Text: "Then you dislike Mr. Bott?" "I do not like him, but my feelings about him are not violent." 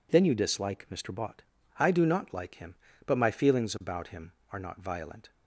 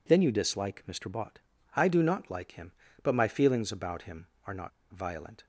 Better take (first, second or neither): first